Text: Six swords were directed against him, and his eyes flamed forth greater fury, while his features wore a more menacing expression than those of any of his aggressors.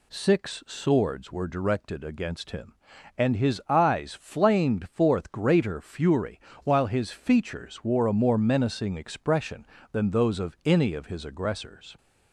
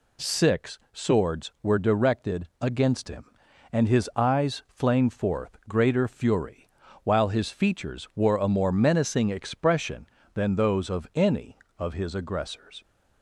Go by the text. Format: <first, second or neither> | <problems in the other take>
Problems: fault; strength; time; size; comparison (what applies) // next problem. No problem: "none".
neither | none